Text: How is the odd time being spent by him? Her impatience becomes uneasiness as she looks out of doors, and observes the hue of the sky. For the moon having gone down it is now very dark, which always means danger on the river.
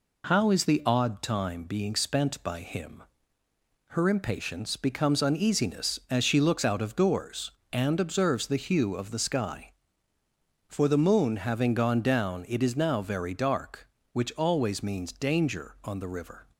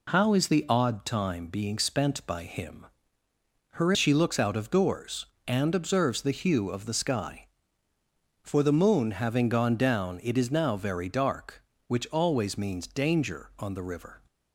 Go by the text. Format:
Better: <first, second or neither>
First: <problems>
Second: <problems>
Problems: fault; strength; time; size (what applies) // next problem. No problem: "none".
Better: first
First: none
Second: skips "impatience becomes uneasiness as"; at 3.9 s